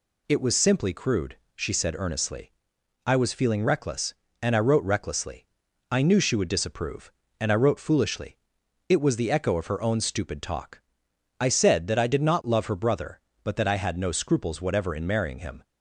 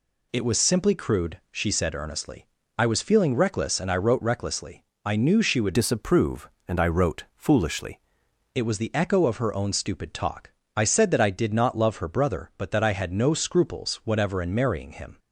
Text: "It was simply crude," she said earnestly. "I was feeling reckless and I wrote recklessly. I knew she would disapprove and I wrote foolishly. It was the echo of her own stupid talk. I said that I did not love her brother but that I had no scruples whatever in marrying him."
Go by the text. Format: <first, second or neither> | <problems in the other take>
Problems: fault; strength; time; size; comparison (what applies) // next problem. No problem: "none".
first | changes voice from "disapprove" to "foolishly"; from 5.7 to 7.9 s; 2.2 s long